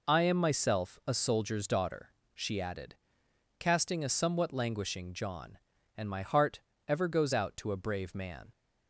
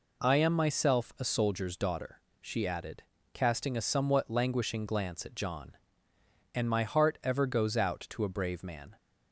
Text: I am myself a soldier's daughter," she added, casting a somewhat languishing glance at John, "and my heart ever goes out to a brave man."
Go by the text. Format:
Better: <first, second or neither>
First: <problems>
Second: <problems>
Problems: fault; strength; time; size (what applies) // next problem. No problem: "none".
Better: second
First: skips "glance at"; at 5.1 s // pauses between "heart" and "ever"; slight; at 6.6 s; 0.26 s long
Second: none